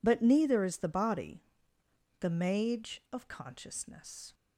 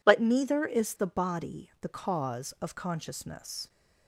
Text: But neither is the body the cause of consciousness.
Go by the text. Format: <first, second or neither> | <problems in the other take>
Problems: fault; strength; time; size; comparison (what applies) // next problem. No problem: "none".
second | pauses between "body" and "the"; noticeable; at 1.4 s; 0.78 s long // says "mage" for "cause"; at 2.2 s